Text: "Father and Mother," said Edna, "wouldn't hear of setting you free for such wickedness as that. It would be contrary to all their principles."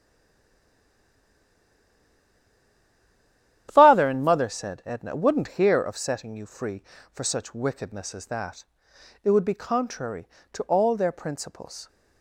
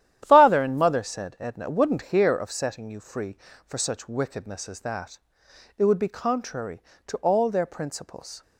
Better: second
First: stays silent before the first word; strong; until 3.6 s; 3.6 s long // starts louder than the rest; strong; until 4.7 s; 11 dB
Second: starts louder than the rest; strong; until 1.2 s; 11 dB

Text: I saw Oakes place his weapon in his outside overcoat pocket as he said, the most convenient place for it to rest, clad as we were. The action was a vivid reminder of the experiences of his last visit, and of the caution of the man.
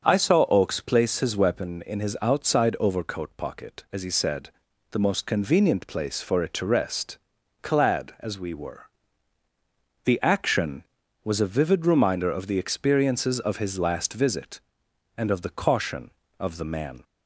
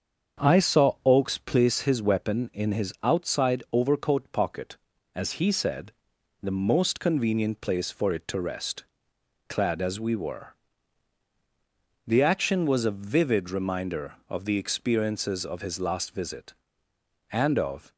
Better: first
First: starts louder than the rest; until 1.1 s; 6.5 dB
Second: starts louder than the rest; strong; until 1.5 s; 7 dB // stops before "the caution of the man"; at 17.9 s

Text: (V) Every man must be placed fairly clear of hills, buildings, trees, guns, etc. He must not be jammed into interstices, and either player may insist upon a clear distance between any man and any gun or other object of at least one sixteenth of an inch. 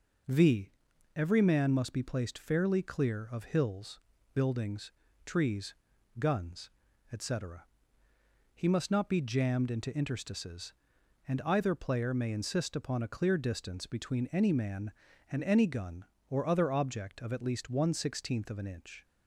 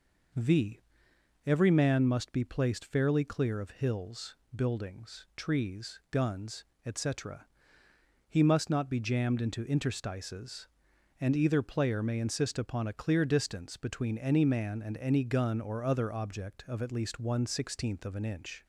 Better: neither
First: none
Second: none

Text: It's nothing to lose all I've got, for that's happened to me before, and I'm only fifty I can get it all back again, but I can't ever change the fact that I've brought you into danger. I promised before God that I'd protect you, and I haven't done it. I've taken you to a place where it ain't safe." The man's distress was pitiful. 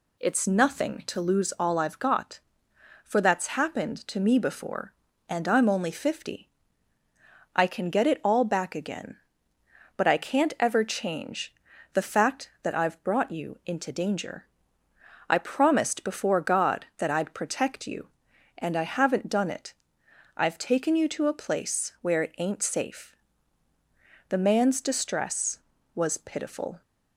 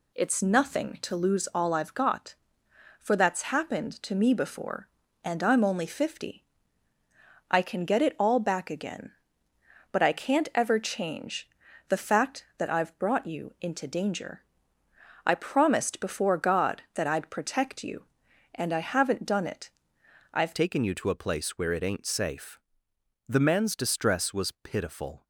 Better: first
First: pauses between "fifty" and "I"; at 6.4 s; 1.0 s long // pauses between "change" and "the"; at 11.5 s; 0.40 s long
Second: pauses between "fifty" and "I"; at 6.4 s; 1.0 s long // pauses between "change" and "the"; at 11.4 s; 0.40 s long // changes voice at "taken"; from 20.5 s on; 4.7 s long

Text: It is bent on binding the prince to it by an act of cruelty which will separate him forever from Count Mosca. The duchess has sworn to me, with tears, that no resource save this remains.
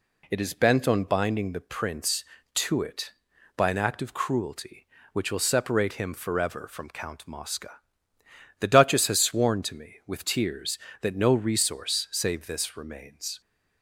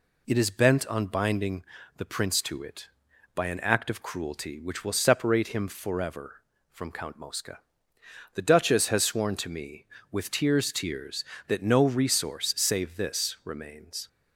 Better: first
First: none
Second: pauses between "binding" and "the"; slight; at 1.6 s; 0.34 s long // says "tears" twice; at 10.7 s

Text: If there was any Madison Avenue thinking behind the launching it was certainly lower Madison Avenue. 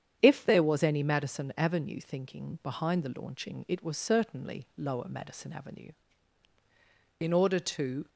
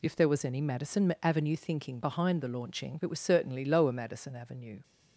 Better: second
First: starts louder than the rest; strong; until 1.2 s; 8.5 dB // goes on to say "In order to"; noticeable; from 7.1 s on; 0.90 s long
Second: none

